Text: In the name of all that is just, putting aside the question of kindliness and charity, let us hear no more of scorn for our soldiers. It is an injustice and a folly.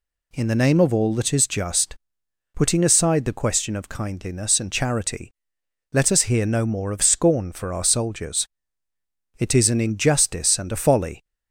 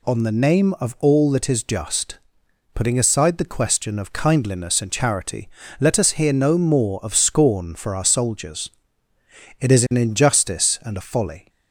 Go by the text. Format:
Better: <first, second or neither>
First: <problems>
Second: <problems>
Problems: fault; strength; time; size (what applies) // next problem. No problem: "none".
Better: first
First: none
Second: says "On" for "In"; at 0.0 s